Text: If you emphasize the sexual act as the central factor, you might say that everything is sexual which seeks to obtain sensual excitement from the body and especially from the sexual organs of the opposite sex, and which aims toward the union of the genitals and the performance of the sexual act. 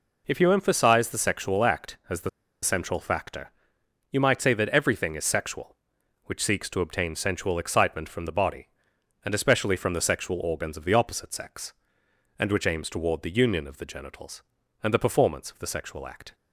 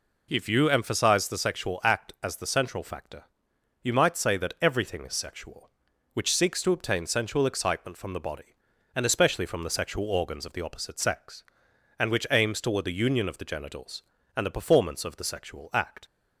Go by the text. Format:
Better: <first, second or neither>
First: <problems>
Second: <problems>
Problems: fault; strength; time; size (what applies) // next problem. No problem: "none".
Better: second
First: pauses between "the" and "central"; slight; at 2.2 s; 0.32 s long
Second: none